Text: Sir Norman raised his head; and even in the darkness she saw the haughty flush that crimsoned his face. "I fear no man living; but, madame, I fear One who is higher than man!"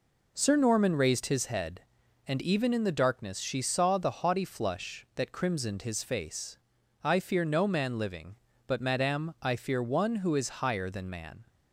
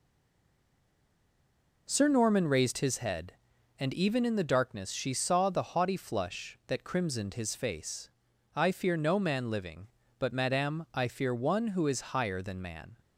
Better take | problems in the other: first | stays silent before the first word; noticeable; until 1.8 s; 1.8 s long

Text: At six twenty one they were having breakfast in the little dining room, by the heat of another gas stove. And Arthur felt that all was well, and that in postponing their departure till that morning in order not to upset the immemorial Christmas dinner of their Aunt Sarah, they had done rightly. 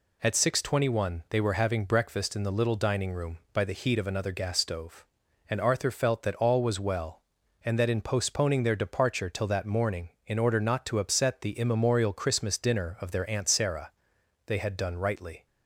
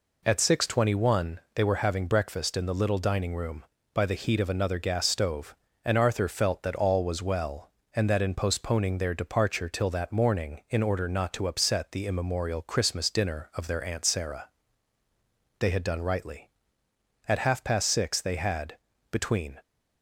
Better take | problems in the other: first | goes on to say "At half past six they had between"; strong; from 17.2 s on; 2.3 s long

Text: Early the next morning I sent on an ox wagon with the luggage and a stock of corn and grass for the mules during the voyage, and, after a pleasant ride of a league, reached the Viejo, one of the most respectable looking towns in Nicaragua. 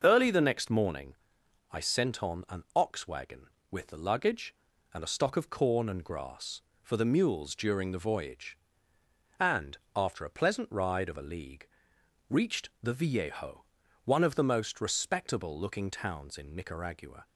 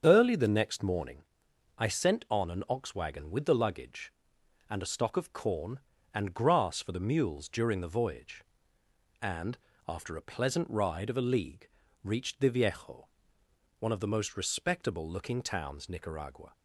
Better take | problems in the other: first | starts louder than the rest; strong; until 1.0 s; 7 dB // pauses between "morning" and "I"; noticeable; at 1.2 s; 0.56 s long; noticeable in the first // skips "in"; at 15.8 s

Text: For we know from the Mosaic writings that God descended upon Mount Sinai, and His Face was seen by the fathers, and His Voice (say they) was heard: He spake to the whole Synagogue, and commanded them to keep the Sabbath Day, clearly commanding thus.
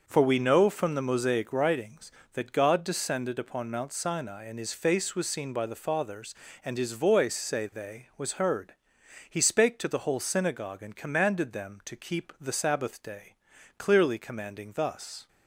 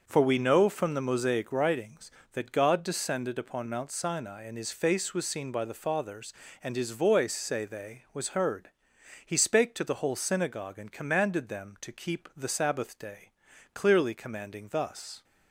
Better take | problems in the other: neither | starts louder than the rest; noticeable; the same in both

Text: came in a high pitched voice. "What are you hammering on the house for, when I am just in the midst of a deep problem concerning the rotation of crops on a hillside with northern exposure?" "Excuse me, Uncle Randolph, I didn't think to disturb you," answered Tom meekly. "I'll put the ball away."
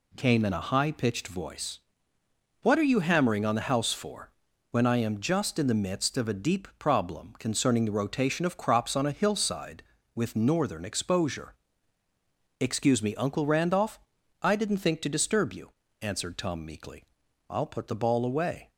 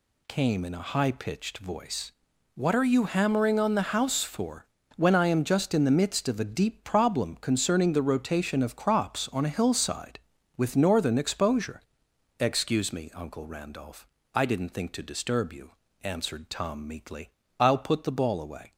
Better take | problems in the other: neither | none

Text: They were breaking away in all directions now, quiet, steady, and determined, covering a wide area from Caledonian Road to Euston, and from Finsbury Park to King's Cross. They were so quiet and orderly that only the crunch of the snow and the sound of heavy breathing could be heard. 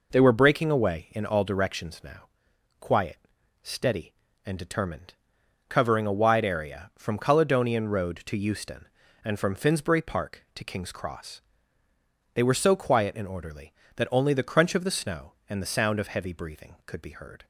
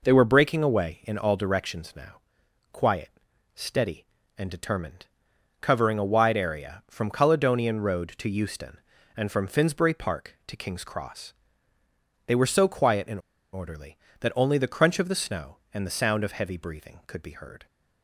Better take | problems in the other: first | pauses between "and" and "orderly"; slight; at 13.1 s; 0.33 s long

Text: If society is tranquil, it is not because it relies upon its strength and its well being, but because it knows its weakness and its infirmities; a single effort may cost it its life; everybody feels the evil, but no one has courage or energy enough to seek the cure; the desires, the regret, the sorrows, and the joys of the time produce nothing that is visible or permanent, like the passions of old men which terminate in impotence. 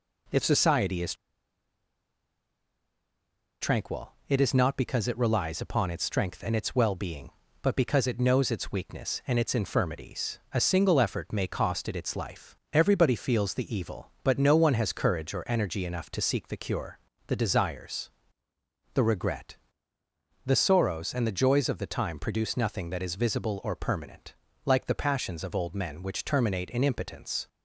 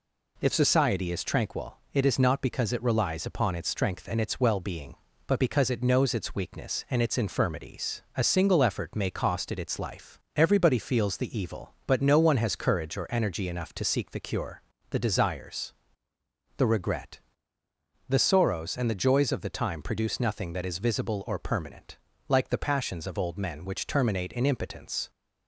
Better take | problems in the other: second | pauses between "is" and "tranquil"; strong; at 1.1 s; 2.4 s long

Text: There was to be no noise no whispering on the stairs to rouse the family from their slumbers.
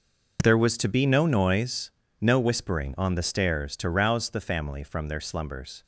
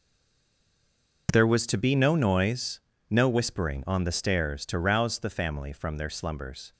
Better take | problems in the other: first | stays silent before the first word; noticeable; until 1.2 s; 1.2 s long // pauses between "noise" and "no"; slight; at 2.8 s; 0.28 s long; slight in the first

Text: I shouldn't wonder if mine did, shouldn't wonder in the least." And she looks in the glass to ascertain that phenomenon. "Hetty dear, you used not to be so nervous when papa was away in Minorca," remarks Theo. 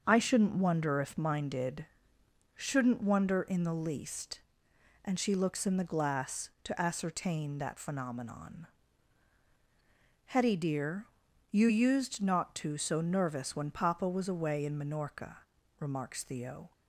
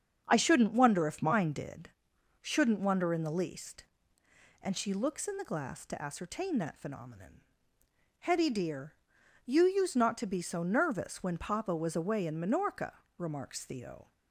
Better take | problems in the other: second | starts louder than the rest; until 1.0 s; 7 dB; also in the second // skips "be"; at 12.7 s

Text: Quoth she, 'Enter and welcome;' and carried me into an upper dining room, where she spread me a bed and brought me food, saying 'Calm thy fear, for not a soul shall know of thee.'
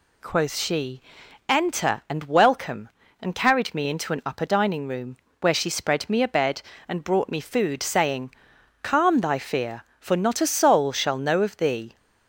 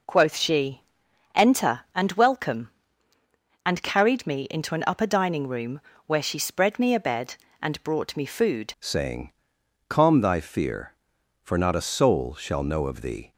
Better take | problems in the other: first | changes voice at "saying"; from 8.7 s on; 4.6 s long // pauses between "saying" and "Calm"; noticeable; at 9.3 s; 0.58 s long; noticeable in the first

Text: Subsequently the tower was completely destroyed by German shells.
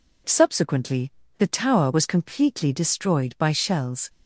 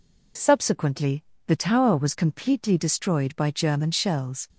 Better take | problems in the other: second | pauses between "Subsequently" and "the"; slight; at 1.1 s; 0.26 s long; slight in the second // skips "German"; at 3.5 s

